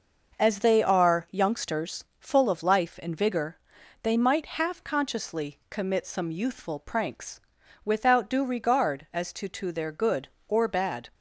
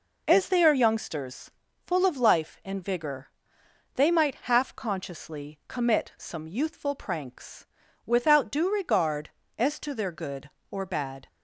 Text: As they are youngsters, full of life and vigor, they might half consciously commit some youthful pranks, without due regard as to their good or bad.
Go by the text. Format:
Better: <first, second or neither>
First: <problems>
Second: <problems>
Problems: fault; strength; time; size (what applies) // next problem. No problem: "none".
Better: second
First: says "to" twice; at 9.4 s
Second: none